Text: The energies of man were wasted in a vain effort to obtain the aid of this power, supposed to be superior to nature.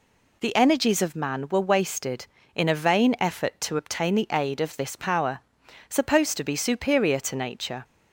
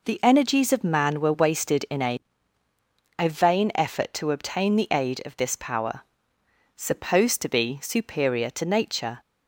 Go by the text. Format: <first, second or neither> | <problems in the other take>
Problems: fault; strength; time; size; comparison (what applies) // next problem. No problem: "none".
first | says "a" twice; at 3.1 s